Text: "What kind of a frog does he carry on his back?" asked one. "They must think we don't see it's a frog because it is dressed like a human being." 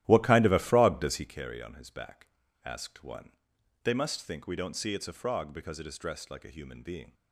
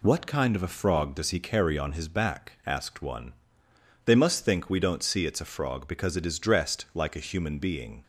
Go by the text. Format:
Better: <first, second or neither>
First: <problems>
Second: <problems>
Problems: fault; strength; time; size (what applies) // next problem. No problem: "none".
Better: second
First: starts louder than the rest; strong; until 1.4 s; 13.5 dB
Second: none